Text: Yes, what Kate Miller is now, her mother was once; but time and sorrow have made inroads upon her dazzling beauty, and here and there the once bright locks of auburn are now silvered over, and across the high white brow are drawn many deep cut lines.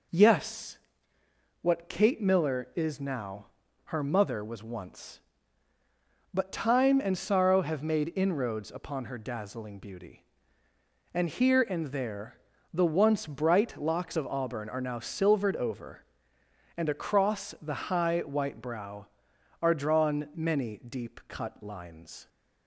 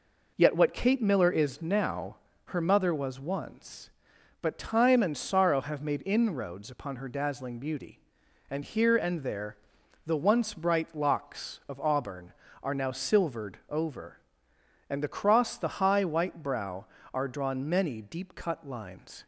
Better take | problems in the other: first | says "Yet" for "Yes"; at 0.3 s // pauses between "there" and "the"; noticeable; at 9.5 s; 0.50 s long; slight in the first

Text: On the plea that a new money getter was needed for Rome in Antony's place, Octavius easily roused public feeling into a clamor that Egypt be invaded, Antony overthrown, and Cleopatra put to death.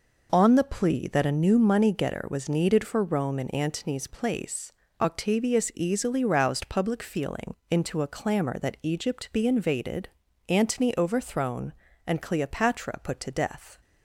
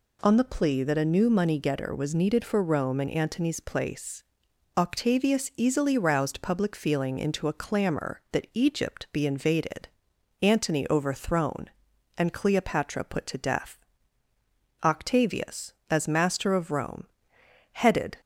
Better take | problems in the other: first | goes on to say "Octavius as master of Rome headed"; strong; from 14.8 s on; 3.3 s long

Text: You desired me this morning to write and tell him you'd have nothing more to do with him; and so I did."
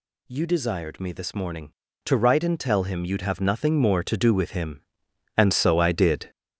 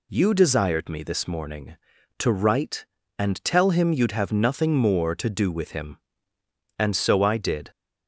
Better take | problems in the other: second | gets louder; throughout; 6.5 dB

